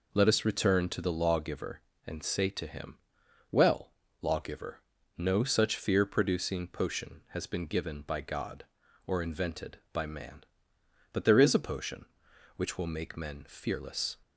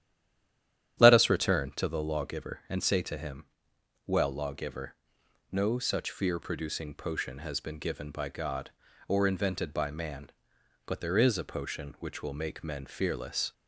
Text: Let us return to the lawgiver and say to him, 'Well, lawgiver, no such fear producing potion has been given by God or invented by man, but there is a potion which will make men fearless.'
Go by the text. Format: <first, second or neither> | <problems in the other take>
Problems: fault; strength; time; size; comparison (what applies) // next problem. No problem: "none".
first | stays silent before the first word; until 0.9 s; 0.9 s long // starts louder than the rest; strong; until 2.0 s; 10 dB